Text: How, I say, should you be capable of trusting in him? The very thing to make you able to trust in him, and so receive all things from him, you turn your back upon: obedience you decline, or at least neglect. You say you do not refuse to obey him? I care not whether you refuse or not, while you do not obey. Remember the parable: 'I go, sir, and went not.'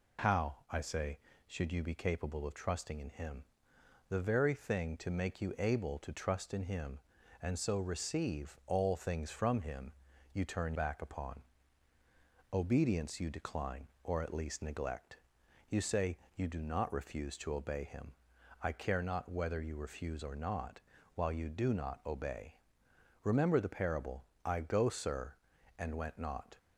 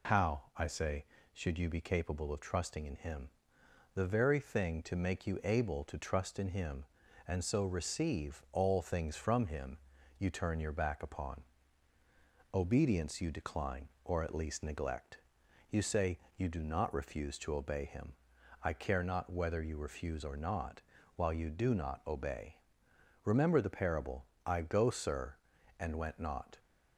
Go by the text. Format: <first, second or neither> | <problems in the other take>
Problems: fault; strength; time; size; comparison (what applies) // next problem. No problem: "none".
second | skips "your"; at 10.7 s // pauses between "say" and "you"; slight; at 16.1 s; 0.18 s long; slight in the second